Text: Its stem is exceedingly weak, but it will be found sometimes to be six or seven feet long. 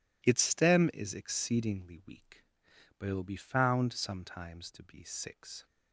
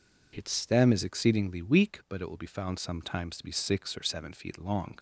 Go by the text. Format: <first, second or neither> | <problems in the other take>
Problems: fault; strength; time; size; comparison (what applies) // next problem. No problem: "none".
second | stops before "or seven feet long"; at 5.6 s